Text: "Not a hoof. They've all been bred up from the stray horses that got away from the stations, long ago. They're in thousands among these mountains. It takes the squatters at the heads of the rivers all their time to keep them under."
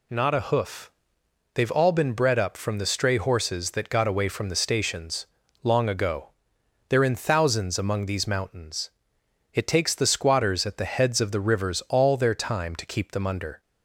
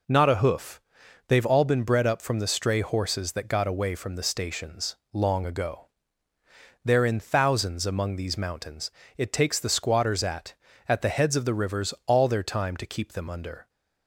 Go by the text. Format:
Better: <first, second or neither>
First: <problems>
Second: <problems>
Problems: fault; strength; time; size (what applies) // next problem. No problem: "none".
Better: first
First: none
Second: says "at" twice; at 10.8 s